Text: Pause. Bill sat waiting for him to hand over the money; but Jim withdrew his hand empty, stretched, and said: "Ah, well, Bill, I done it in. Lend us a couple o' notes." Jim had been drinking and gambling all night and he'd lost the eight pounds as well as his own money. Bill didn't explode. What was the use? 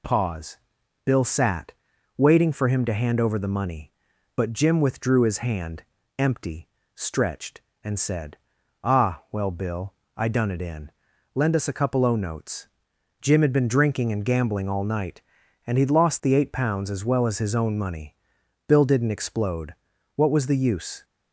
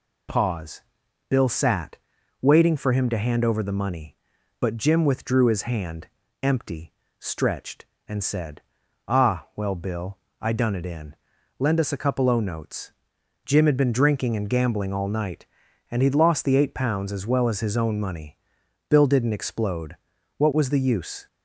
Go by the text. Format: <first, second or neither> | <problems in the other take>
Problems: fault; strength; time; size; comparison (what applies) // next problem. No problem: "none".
neither | pauses between "sat" and "waiting"; the same in both // pauses between "hand" and "empty"; slight; the same in both